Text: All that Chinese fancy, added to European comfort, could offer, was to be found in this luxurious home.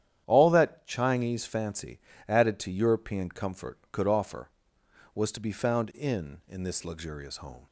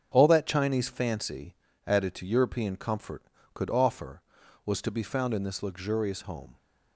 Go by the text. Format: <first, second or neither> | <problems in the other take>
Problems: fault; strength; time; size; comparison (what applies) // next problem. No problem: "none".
second | starts louder than the rest; strong; until 1.2 s; 10 dB; strong in the second // says "in" twice; at 6.4 s